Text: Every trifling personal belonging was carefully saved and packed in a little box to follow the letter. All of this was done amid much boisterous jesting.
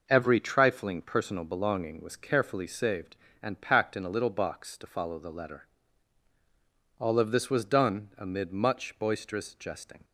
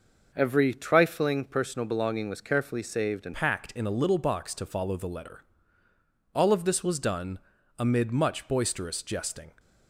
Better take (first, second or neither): first